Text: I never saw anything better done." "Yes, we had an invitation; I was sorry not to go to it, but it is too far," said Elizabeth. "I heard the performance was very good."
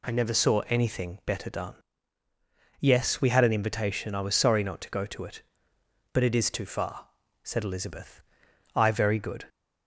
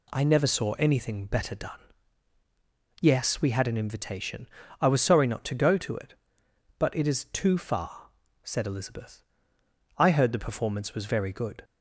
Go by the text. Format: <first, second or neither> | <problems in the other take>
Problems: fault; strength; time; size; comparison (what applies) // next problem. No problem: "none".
second | skips "heard the performance was"; at 8.9 s